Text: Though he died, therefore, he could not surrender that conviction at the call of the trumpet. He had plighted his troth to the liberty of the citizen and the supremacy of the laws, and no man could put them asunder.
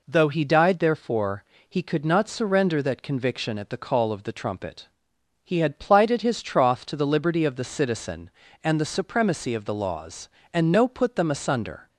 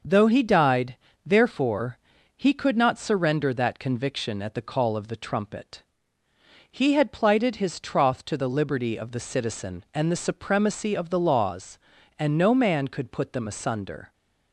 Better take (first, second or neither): second